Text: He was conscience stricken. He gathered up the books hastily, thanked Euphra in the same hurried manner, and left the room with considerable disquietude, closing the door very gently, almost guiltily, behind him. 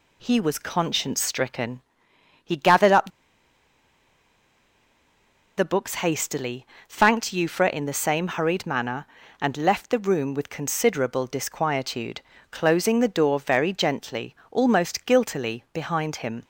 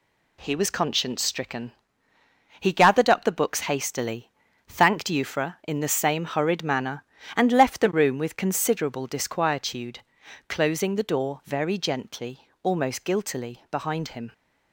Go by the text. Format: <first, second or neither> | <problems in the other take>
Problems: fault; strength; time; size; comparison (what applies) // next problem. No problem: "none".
second | pauses between "up" and "the"; strong; at 3.0 s; 2.4 s long